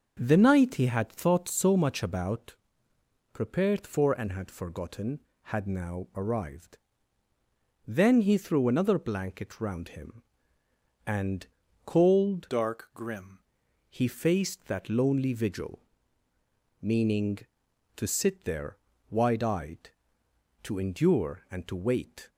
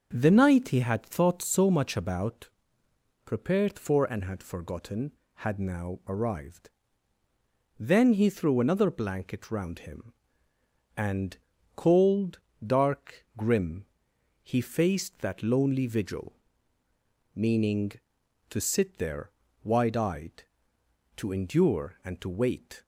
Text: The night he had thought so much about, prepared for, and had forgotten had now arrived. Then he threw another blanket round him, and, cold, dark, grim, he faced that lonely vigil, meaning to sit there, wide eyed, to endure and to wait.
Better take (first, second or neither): second